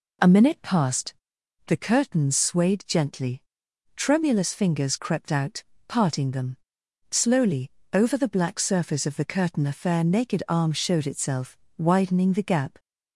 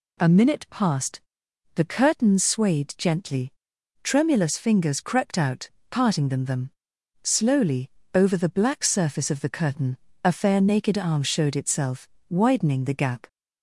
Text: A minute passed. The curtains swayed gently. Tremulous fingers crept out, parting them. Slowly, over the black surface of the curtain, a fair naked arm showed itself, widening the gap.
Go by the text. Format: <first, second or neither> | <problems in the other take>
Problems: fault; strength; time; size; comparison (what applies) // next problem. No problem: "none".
first | says "them" twice; at 6.4 s